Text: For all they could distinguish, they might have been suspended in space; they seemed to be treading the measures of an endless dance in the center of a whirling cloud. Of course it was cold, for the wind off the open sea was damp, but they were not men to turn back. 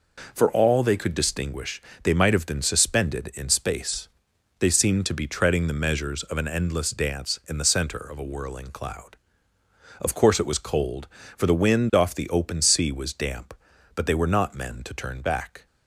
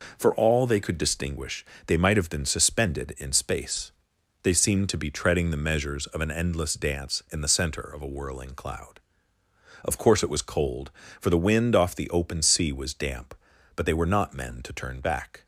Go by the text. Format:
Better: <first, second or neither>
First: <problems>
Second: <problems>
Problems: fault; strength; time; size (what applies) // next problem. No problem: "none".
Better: neither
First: none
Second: none